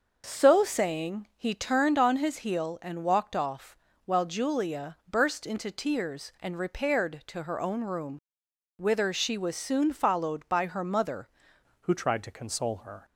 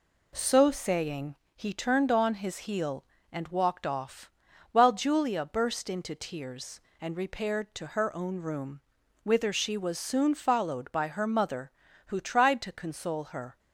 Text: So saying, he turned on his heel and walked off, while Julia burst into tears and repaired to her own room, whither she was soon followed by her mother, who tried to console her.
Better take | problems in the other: second | starts louder than the rest; until 1.2 s; 6 dB // changes voice at "who"; from 11.8 s on; 1.2 s long

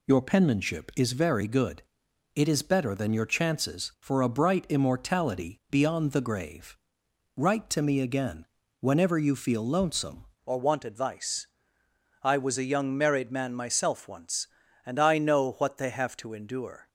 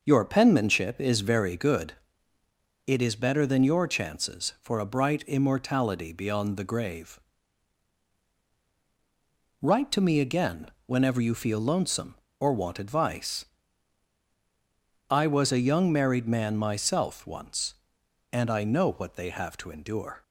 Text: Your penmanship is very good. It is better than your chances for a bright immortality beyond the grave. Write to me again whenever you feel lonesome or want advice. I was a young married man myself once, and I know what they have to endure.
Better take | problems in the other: second | pauses between "again" and "whenever"; slight; at 8.4 s; 0.36 s long; slight in the second // changes voice at "or"; from 10.4 s on; 6.4 s long

